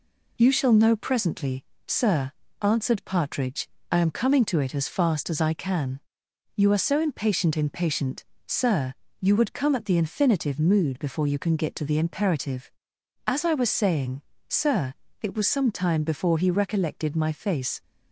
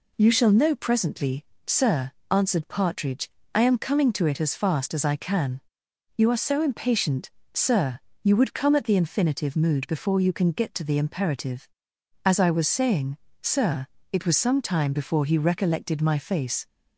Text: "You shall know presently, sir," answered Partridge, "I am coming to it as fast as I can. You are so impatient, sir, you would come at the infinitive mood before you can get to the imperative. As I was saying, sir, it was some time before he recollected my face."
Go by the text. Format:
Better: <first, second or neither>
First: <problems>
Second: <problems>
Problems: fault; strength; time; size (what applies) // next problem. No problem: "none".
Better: second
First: says "impatient" twice; at 7.5 s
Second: none